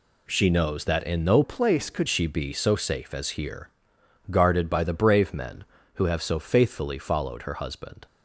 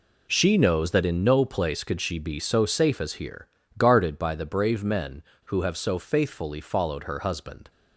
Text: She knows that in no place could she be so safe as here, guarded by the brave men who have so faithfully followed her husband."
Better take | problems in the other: second | changes voice from "place" to "could"; from 1.4 to 2.0 s; 0.6 s long

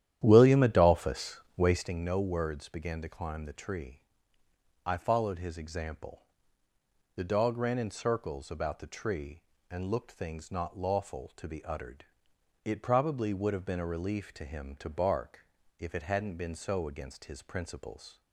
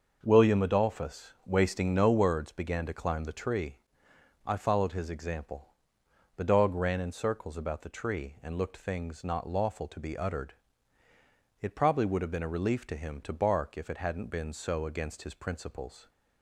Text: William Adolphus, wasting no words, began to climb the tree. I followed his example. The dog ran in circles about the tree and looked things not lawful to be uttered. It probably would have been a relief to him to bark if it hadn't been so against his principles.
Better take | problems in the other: second | starts louder than the rest; strong; until 1.9 s; 11 dB // pauses between "bark" and "if"; slight; at 15.4 s; 0.36 s long

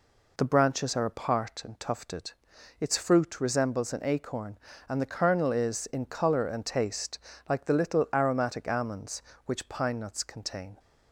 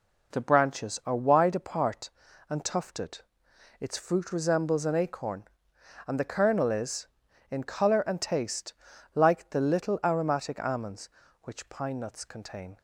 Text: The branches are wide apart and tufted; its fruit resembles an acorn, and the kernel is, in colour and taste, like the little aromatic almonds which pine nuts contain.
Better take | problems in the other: second | skips "wide"; at 1.0 s

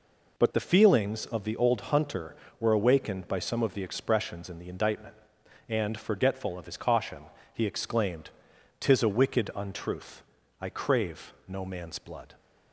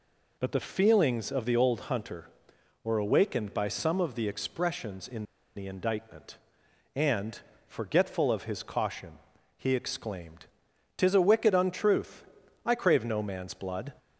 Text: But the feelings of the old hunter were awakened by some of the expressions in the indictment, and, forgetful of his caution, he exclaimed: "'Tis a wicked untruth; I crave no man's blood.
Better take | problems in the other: first | pauses between "in" and "the"; slight; at 5.2 s; 0.32 s long

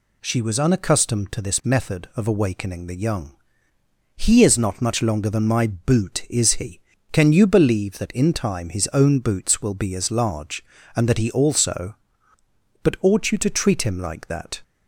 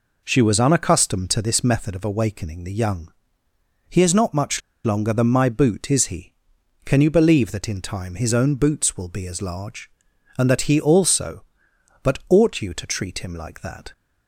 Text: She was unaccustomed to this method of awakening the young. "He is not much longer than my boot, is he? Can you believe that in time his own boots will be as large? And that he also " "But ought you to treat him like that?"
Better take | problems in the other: first | pauses between "much" and "longer"; slight; at 4.6 s; 0.25 s long

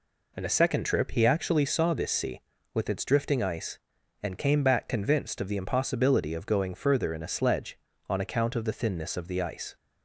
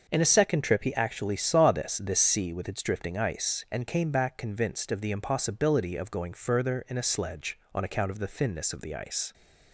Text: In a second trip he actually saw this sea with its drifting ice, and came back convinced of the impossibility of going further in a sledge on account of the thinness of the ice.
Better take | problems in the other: first | starts louder than the rest; until 1.0 s; 6 dB // says "this" twice; at 1.9 s

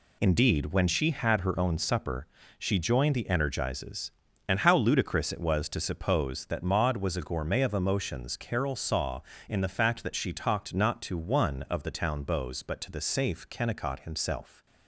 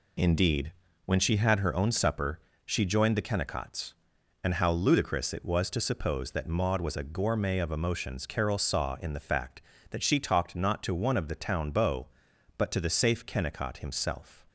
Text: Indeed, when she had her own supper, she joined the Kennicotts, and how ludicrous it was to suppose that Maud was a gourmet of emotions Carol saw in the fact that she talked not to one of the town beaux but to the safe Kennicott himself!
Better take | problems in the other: second | says "Energizes" for "Kennicotts"; at 3.2 s

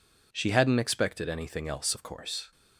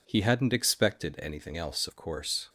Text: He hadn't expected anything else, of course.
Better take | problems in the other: second | says "She" for "He"; at 0.3 s

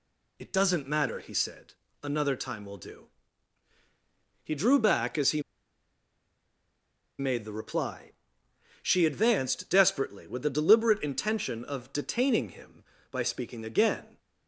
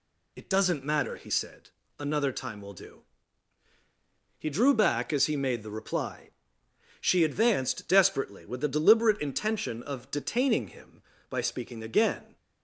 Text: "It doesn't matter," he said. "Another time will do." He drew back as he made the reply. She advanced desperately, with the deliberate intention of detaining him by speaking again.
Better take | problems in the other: second | pauses between "he" and "made"; strong; at 5.4 s; 1.7 s long

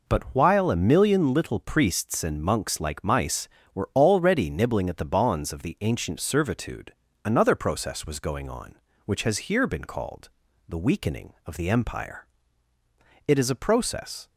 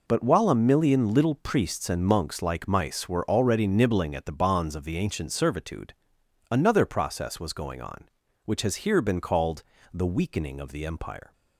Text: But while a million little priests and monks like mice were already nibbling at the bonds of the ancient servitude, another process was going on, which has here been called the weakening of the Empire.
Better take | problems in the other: second | pauses between "called" and "the"; slight; at 10.2 s; 0.36 s long; slight in the second // goes on to say "It is a process"; noticeable; from 13.2 s on; 1.0 s long

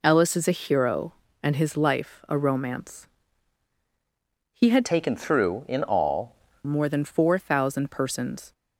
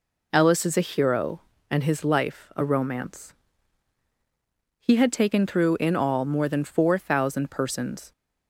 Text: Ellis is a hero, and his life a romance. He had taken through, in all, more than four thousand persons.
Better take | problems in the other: second | changes voice from "taken" to "all"; from 4.8 to 6.3 s; 1.5 s long

